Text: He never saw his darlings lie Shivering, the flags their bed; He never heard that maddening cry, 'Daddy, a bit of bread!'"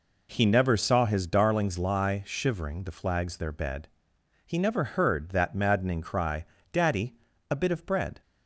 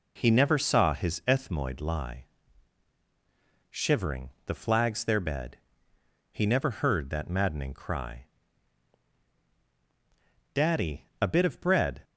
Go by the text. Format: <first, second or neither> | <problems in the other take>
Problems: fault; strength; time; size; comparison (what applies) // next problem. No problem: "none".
first | says "ethmoid" for "darlings"; at 1.2 s // pauses between "lie" and "Shivering"; strong; at 2.2 s; 1.4 s long